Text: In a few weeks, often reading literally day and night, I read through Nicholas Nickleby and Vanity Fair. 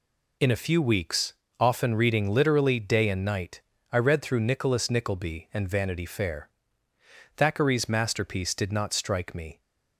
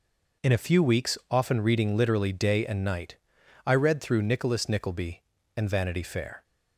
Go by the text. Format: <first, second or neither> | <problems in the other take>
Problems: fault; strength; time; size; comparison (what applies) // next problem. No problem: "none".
second | goes on to say "Thackeray's masterpiece did not strike me"; strong; from 7.3 s on; 2.2 s long